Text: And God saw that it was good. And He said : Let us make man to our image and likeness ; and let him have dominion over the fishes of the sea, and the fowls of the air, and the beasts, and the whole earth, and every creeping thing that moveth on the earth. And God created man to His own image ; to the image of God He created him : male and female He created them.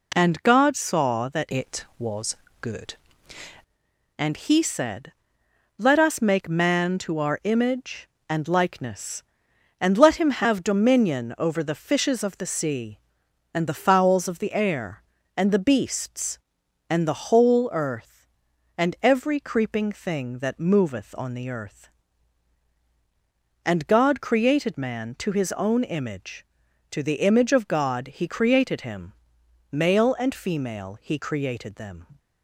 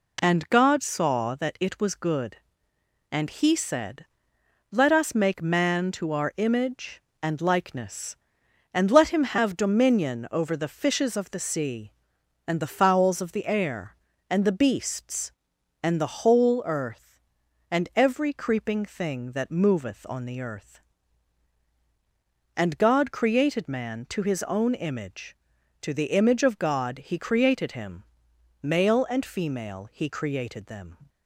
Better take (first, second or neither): second